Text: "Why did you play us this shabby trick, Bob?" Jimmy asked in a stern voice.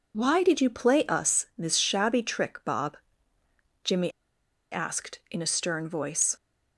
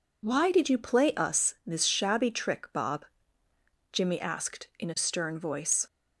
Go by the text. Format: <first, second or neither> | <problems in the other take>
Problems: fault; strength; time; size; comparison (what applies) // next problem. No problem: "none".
second | pauses between "Jimmy" and "asked"; noticeable; at 4.0 s; 0.61 s long